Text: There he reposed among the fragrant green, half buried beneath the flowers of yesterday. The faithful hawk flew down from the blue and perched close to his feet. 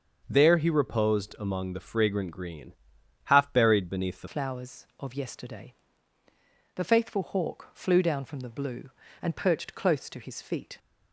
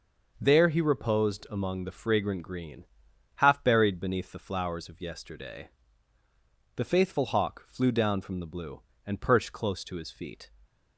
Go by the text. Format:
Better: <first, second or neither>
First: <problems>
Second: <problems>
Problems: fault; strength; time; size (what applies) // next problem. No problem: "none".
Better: second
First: starts louder than the rest; until 1.2 s; 6.5 dB // changes voice at "flowers"; from 4.2 s on; 6.5 s long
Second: none